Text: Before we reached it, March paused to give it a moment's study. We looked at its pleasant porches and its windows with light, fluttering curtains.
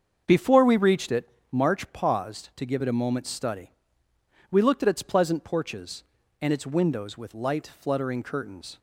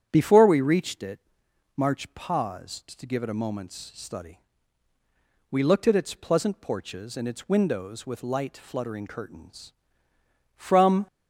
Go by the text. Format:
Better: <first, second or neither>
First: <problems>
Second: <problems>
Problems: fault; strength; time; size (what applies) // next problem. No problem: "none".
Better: first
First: starts louder than the rest; until 1.2 s; 7 dB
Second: starts louder than the rest; strong; until 1.1 s; 9 dB // goes on to say "From"; from 10.5 s on; 0.50 s long